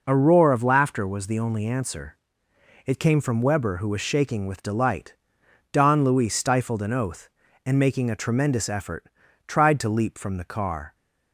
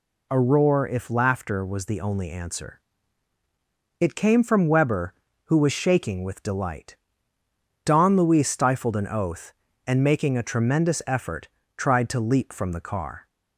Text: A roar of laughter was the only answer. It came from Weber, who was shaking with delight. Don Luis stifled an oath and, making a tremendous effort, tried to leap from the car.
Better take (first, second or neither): first